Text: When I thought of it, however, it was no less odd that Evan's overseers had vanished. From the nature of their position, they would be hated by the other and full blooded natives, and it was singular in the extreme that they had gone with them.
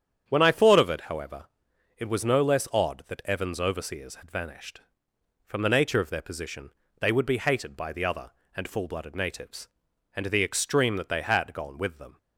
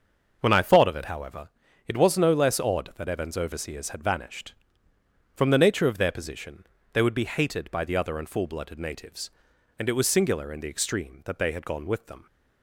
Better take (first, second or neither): second